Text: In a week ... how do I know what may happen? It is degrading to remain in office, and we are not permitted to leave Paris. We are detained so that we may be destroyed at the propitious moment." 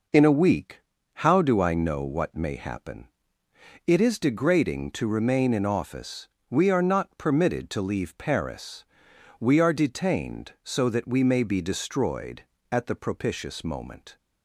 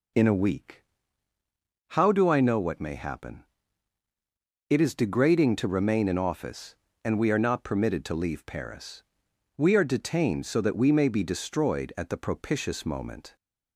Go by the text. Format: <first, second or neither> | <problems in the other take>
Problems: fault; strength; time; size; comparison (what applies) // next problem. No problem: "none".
second | skips "and"; at 6.3 s